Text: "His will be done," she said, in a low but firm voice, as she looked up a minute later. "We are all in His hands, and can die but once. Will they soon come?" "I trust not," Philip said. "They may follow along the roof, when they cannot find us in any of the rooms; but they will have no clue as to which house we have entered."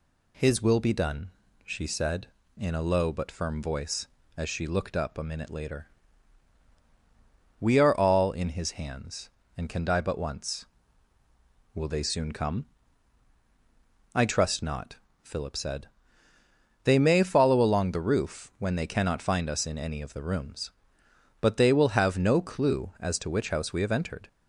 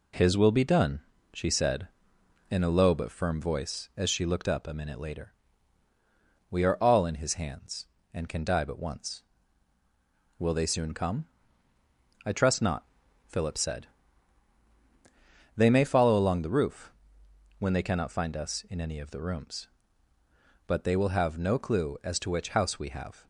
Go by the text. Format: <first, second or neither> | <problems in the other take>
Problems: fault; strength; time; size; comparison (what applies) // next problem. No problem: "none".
first | stops before "entered"; at 23.2 s